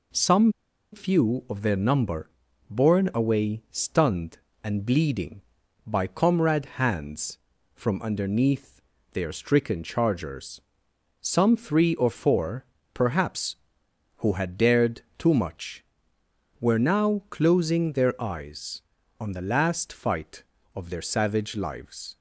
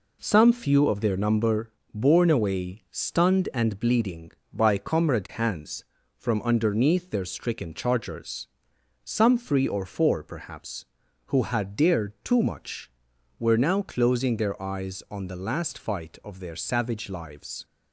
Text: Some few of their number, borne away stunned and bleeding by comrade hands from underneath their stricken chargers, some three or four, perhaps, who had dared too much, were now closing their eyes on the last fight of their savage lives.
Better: second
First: pauses between "Some" and "few"; at 0.5 s; 0.41 s long // pauses between "underneath" and "their"; slight; at 8.8 s; 0.32 s long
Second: none

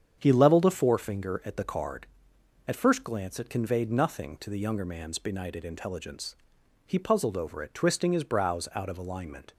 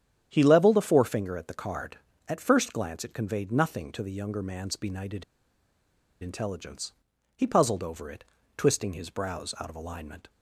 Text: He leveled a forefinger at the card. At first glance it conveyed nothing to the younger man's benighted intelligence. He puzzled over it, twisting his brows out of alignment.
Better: first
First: starts louder than the rest; strong; until 1.2 s; 8 dB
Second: starts louder than the rest; strong; until 1.3 s; 9 dB // pauses between "benighted" and "intelligence"; at 5.2 s; 0.98 s long

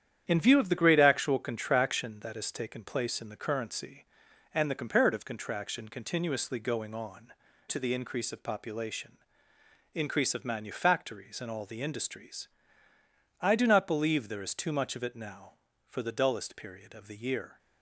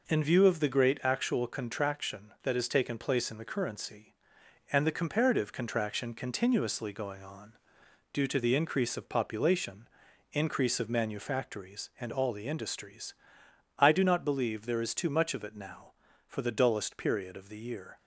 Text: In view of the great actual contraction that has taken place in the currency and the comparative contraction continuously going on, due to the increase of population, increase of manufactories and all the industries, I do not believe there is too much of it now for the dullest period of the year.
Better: second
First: starts louder than the rest; strong; until 1.2 s; 9.5 dB // skips "due"; at 7.4 s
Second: none

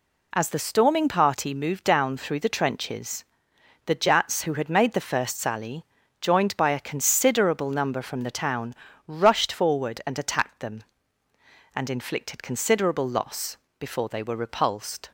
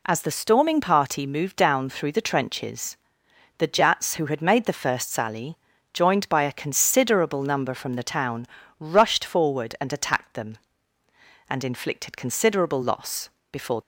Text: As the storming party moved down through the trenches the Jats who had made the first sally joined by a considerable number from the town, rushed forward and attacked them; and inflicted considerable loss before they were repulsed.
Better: first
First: pauses between "trenches" and "the"; noticeable; at 3.2 s; 0.60 s long // pauses between "sally" and "joined"; slight; at 5.8 s; 0.36 s long // pauses between "loss" and "before"; slight; at 13.5 s; 0.22 s long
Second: pauses between "trenches" and "the"; noticeable; at 2.9 s; 0.60 s long // pauses between "sally" and "joined"; slight; at 5.5 s; 0.36 s long // pauses between "loss" and "before"; slight; at 13.2 s; 0.22 s long // stops before "they were repulsed"; at 13.8 s

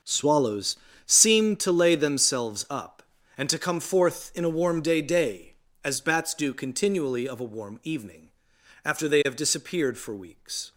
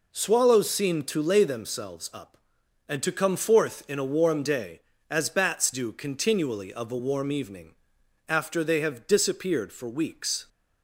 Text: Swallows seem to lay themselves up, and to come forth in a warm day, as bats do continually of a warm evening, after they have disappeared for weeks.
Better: second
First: starts louder than the rest; until 1.3 s; 6.5 dB // pauses between "Swallows" and "seem"; slight; at 0.7 s; 0.30 s long // says "day" twice; at 4.9 s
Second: none

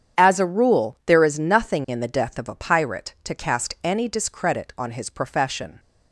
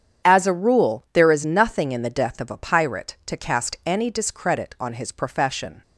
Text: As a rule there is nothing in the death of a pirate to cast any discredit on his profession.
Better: neither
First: starts louder than the rest; strong; until 1.2 s; 8.5 dB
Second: starts louder than the rest; strong; until 1.3 s; 8.5 dB

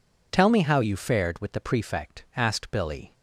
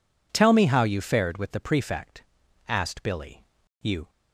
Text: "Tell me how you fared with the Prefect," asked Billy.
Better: first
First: none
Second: goes on to say "You"; slight; from 3.8 s on; 0.28 s long

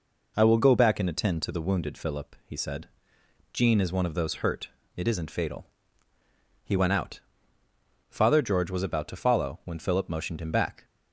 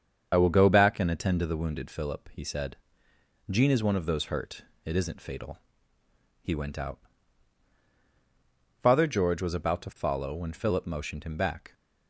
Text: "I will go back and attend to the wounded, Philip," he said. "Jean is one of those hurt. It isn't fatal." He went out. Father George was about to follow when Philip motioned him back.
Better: first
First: none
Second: loses the start of "I"; at 0.3 s; 30 ms // starts louder than the rest; strong; until 1.3 s; 7 dB

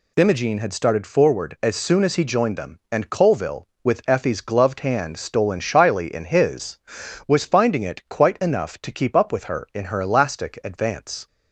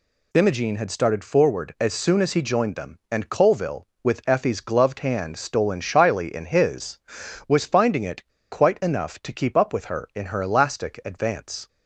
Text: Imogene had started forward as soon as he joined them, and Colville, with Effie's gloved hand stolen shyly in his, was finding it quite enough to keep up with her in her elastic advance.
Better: first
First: none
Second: pauses between "it" and "quite"; slight; at 8.2 s; 0.27 s long

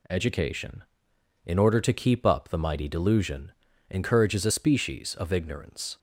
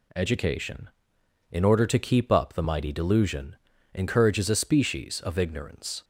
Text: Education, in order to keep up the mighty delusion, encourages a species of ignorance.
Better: neither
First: none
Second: none

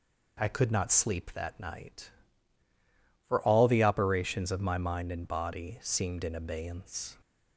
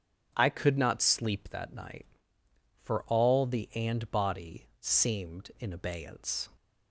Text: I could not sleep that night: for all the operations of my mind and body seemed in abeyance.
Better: first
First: none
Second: starts louder than the rest; strong; until 1.3 s; 8.5 dB // skips "operations of my mind"; at 3.7 s

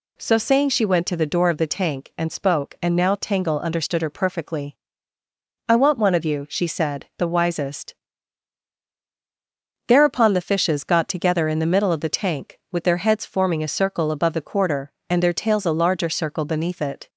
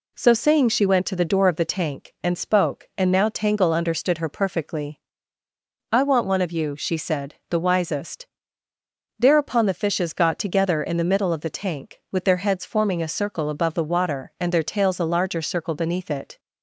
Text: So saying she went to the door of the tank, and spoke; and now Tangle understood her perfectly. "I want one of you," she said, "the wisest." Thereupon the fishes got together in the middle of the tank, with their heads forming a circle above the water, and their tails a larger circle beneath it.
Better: second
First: says "quarter" for "water"; at 14.4 s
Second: none

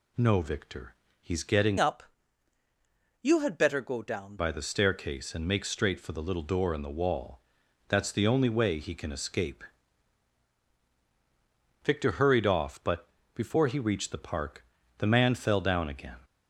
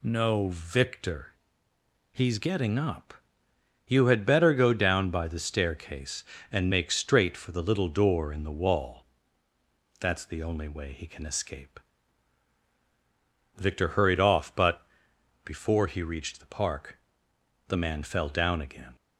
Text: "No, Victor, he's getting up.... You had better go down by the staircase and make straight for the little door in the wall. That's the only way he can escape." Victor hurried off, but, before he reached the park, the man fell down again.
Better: second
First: changes voice from "up" to "down"; from 1.7 to 4.3 s; 2.6 s long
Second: none

